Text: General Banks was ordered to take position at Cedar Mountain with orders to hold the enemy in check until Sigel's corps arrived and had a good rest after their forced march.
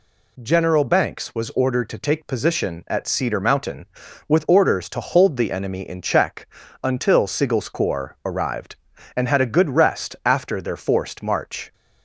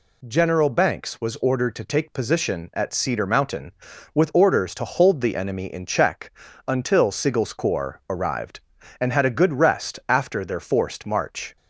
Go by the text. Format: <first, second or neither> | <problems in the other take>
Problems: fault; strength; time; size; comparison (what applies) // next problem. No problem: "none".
neither | pauses between "check" and "until"; the same in both